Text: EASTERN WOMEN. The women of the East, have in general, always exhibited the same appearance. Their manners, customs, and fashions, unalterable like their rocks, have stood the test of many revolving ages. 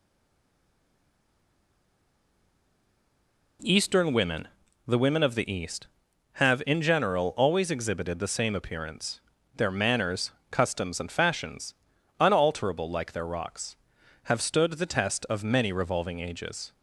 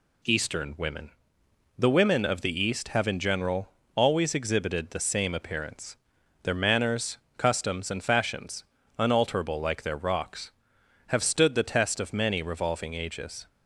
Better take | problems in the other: second | stays silent before the first word; strong; until 3.5 s; 3.5 s long

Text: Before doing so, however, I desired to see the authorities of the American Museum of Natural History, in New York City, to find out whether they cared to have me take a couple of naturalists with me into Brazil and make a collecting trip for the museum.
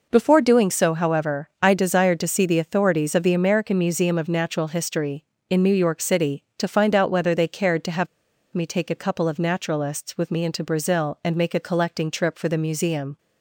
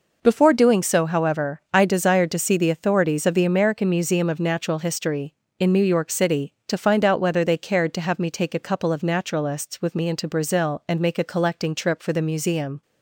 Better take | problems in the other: second | pauses between "have" and "me"; noticeable; at 8.0 s; 0.46 s long

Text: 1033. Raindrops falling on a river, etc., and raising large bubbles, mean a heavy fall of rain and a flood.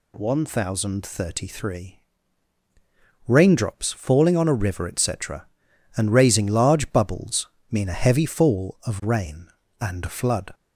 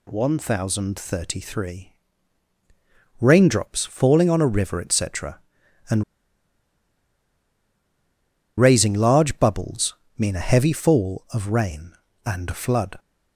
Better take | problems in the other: first | pauses between "and" and "raising"; strong; at 6.0 s; 2.5 s long

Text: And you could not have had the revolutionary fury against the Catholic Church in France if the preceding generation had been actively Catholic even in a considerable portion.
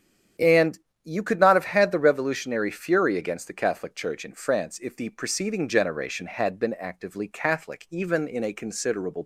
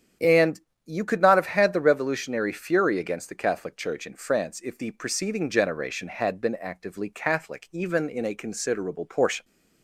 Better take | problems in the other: second | starts louder than the rest; strong; until 1.6 s; 9 dB; strong in the second // pauses between "And" and "you"; slight; at 0.7 s; 0.26 s long; slight in the second // stops before "portion"; at 9.2 s

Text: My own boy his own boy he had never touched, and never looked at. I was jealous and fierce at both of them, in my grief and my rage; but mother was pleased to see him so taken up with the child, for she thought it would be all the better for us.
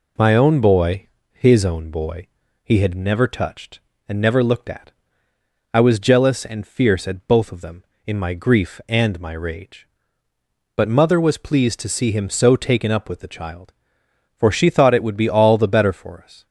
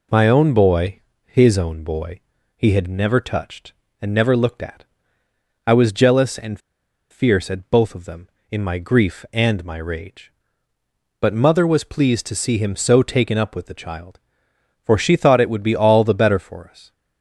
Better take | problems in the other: first | pauses between "boy" and "his"; slight; at 1.0 s; 0.24 s long; slight in the first // pauses between "boy" and "he"; slight; at 2.2 s; 0.36 s long; slight in the first // pauses between "and" and "fierce"; noticeable; at 6.5 s; 0.51 s long

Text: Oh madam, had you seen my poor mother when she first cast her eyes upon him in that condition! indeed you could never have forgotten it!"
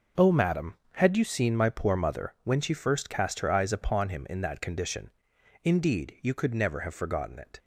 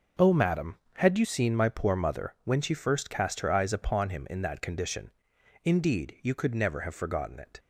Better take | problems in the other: neither | none

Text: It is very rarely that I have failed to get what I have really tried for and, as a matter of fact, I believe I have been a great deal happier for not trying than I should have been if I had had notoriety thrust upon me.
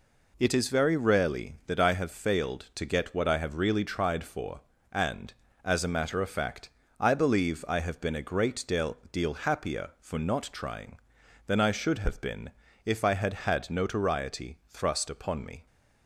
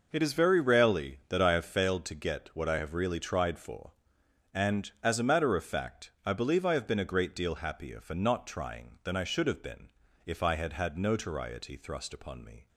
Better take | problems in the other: second | says "deal" twice; at 9.1 s // pauses between "been" and "if"; slight; at 12.4 s; 0.34 s long; slight in the second

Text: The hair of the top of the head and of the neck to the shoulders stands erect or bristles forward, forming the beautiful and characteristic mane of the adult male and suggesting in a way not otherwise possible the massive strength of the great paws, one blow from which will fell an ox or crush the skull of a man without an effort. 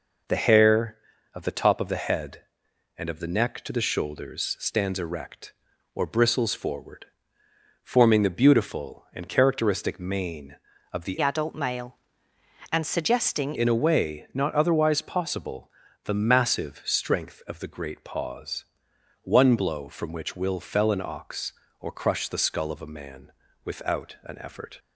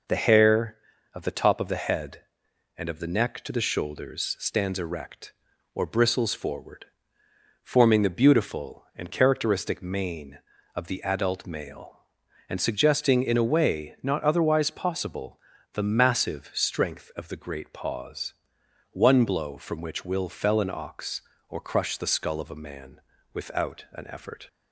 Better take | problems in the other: second | changes voice from "adult" to "suggesting"; from 11.2 to 13.5 s; 2.3 s long // pauses between "possible" and "the"; slight; at 15.7 s; 0.34 s long; slight in the second // pauses between "man" and "without"; slight; at 23.3 s; 0.32 s long; slight in the second

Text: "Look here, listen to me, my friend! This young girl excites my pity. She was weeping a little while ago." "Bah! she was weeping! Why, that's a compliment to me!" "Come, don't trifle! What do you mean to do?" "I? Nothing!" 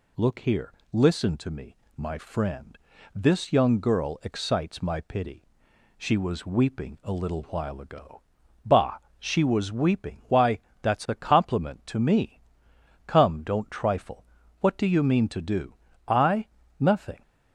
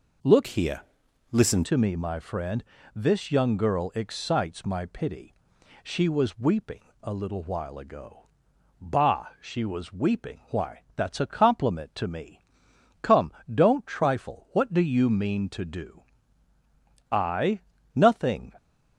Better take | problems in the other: first | changes voice from "here" to "listen"; from 0.4 to 1.6 s; 1.2 s long // pauses between "weeping" and "a"; slight; at 6.8 s; 0.20 s long

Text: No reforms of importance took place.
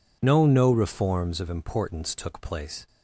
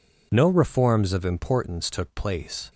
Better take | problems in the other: second | says "No" twice; at 0.4 s

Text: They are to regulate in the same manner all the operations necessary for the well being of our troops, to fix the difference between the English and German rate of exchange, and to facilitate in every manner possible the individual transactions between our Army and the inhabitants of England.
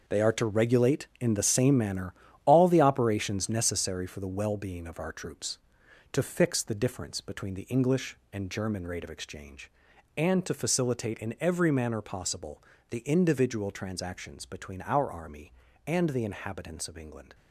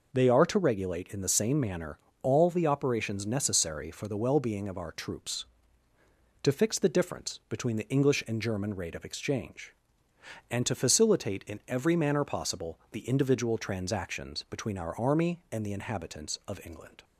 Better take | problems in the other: second | gets quieter; strong; throughout; 10 dB // pauses between "manner" and "all"; slight; at 2.1 s; 0.32 s long; slight in the second // pauses between "possible" and "the"; slight; at 12.6 s; 0.28 s long

